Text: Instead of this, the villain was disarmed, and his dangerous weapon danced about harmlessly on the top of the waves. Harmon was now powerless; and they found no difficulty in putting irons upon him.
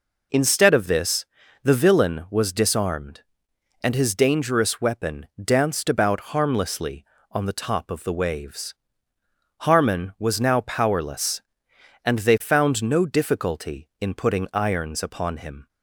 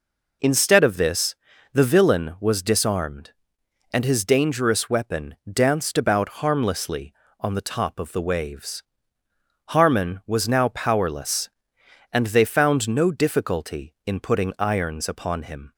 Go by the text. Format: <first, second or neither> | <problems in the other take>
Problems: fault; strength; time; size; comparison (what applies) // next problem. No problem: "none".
neither | pauses between "weapon" and "danced"; slight; the same in both